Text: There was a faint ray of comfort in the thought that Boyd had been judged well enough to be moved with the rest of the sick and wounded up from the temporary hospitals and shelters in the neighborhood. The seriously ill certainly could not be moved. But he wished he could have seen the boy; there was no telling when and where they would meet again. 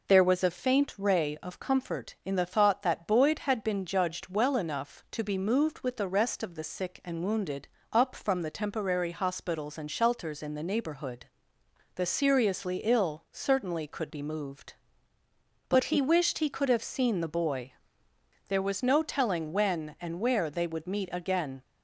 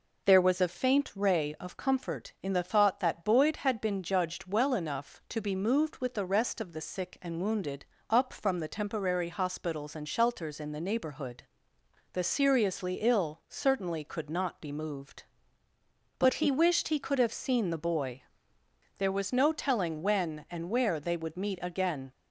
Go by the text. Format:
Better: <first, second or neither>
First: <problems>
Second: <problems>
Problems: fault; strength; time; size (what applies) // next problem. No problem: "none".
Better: second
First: pauses between "wounded" and "up"; slight; at 7.6 s; 0.22 s long // skips "not"; at 14.1 s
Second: pauses between "wounded" and "up"; slight; at 7.8 s; 0.22 s long